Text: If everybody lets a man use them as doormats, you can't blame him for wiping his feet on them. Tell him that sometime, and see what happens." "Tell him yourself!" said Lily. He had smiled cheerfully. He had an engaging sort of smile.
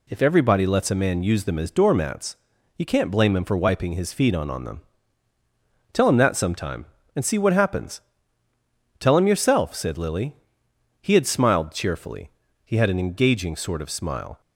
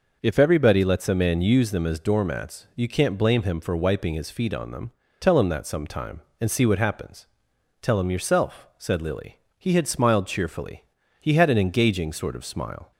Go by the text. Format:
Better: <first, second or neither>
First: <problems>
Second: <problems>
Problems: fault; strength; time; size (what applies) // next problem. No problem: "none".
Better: second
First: says "on" twice; at 4.4 s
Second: none